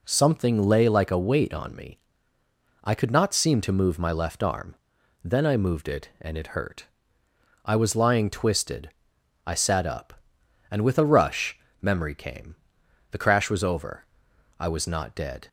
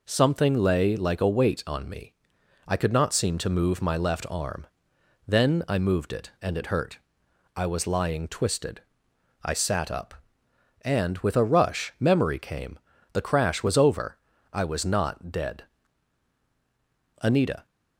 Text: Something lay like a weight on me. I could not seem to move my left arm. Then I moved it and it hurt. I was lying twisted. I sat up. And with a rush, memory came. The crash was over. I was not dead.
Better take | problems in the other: first | goes on to say "Anita"; slight; from 17.2 s on; 0.44 s long

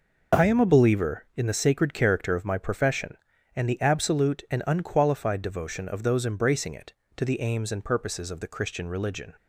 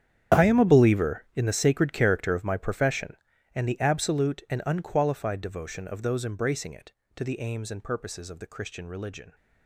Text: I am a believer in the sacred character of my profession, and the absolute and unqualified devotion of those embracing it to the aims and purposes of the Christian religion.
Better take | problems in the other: first | gets quieter; strong; throughout; 15.5 dB

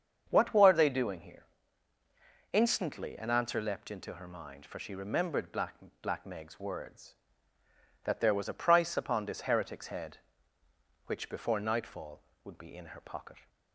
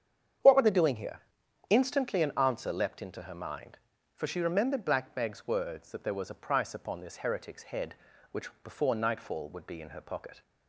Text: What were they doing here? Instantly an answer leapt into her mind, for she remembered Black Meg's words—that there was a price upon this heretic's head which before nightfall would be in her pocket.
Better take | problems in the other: second | starts louder than the rest; strong; until 1.3 s; 7 dB; strong in the second // says "Black" twice; at 6.0 s

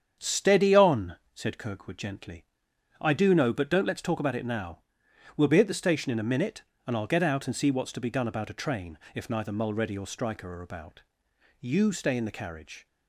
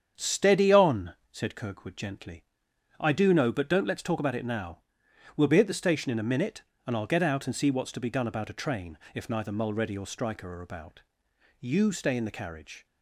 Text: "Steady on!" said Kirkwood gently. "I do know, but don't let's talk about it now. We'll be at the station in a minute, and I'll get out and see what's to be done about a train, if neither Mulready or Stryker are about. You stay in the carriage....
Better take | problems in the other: neither | starts louder than the rest; strong; the same in both

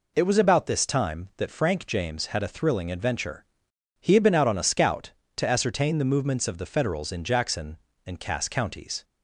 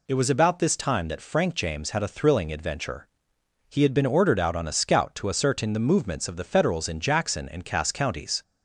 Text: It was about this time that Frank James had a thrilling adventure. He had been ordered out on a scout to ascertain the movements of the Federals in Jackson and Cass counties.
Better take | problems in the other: second | skips "ordered"; at 4.3 s

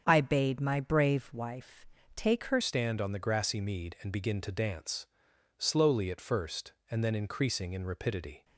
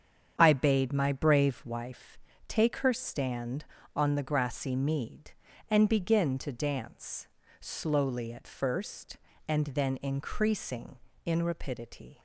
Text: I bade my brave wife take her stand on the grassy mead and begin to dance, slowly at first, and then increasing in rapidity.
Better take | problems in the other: second | starts louder than the rest; strong; until 1.0 s; 7.5 dB; strong in the second // pauses between "wife" and "take"; slight; at 1.8 s; 0.28 s long; slight in the second // changes voice at "stand"; from 2.6 s on; 5.8 s long

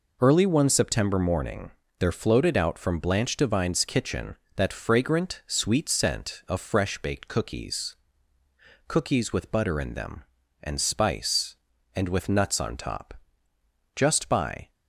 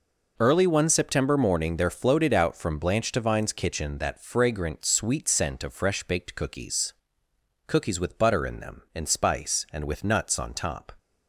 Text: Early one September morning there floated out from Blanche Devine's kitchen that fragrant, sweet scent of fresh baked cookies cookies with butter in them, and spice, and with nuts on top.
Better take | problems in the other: second | pauses between "morning" and "there"; slight; at 1.7 s; 0.28 s long // pauses between "cookies" and "cookies"; noticeable; at 7.9 s; 0.92 s long; noticeable in the second // goes on to say "Just by"; noticeable; from 13.9 s on; 0.76 s long

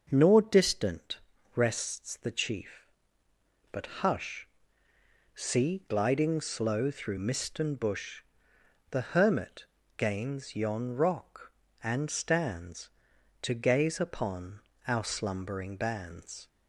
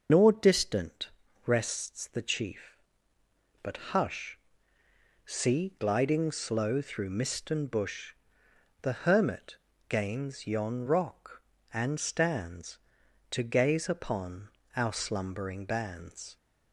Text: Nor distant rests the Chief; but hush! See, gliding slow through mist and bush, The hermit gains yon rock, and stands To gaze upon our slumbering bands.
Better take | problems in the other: first | loses the start of "Nor"; at 0.0 s; 110 ms // starts louder than the rest; noticeable; until 1.4 s; 6 dB; also in the first // pauses between "distant" and "rests"; slight; at 1.0 s; 0.36 s long; slight in the first // pauses between "hermit" and "gains"; slight; at 9.5 s; 0.32 s long; slight in the first // pauses between "upon" and "our"; slight; at 14.5 s; 0.26 s long; slight in the first

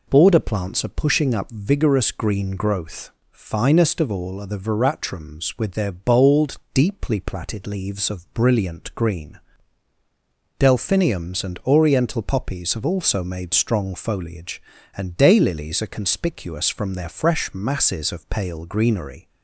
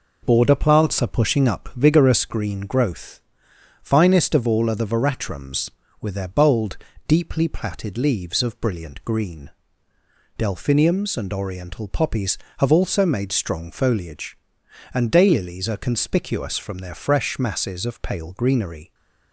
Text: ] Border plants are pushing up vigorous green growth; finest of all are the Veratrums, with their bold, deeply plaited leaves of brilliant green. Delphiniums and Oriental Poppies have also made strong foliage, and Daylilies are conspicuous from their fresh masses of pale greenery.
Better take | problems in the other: neither | none

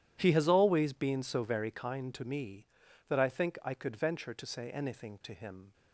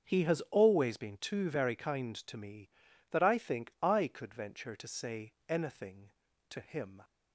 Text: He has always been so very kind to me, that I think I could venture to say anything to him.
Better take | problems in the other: first | starts louder than the rest; until 1.1 s; 7 dB // says "too" for "so"; at 1.1 s // pauses between "say" and "anything"; slight; at 5.3 s; 0.16 s long

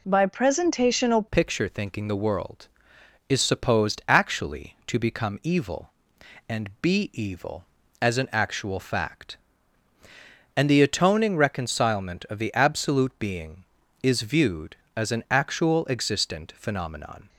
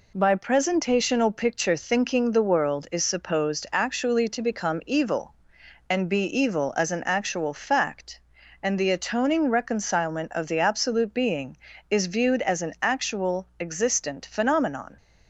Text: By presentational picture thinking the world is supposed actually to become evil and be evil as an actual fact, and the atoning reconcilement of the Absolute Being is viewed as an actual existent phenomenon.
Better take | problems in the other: second | changes voice at "picture"; from 1.3 s on; 15.9 s long

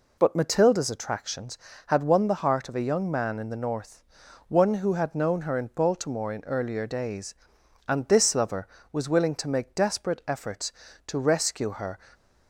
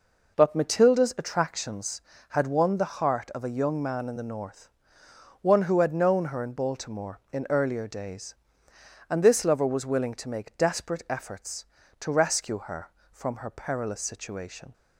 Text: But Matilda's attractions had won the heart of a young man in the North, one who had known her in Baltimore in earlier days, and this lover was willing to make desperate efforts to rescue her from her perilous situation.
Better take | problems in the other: second | stops before "from her perilous situation"; at 12.1 s

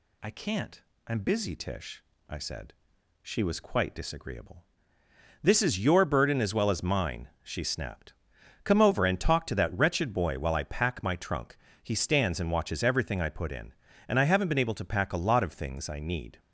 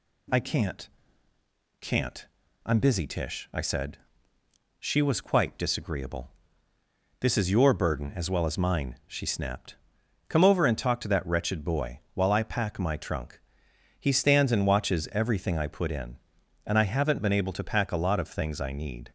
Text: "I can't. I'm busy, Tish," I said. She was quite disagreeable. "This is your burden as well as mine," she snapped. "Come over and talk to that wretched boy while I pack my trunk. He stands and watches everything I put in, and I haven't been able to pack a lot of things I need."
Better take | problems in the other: first | says "can't" twice; at 1.8 s

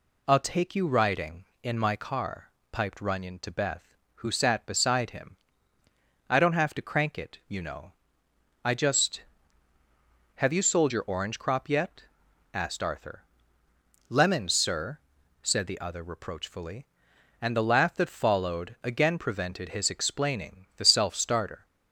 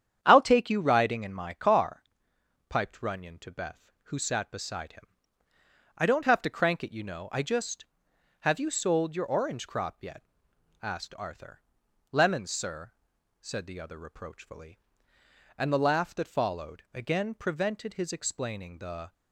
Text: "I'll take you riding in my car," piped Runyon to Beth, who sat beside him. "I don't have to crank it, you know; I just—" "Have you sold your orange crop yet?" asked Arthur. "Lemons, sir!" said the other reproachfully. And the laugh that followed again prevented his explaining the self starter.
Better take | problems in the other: first | starts louder than the rest; strong; until 1.2 s; 9 dB // stops before "self starter"; at 19.1 s

